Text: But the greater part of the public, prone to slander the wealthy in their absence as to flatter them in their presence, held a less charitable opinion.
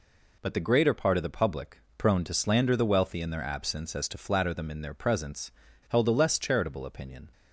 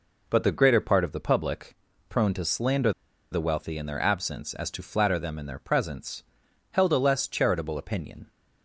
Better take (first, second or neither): first